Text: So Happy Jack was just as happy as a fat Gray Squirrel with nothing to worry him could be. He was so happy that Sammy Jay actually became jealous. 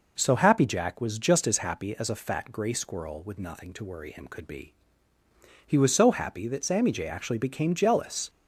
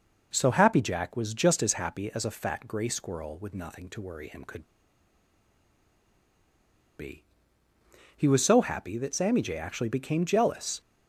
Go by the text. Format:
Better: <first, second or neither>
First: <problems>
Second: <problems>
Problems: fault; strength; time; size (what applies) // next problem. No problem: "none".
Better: first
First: none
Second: pauses between "could" and "be"; strong; at 4.6 s; 2.3 s long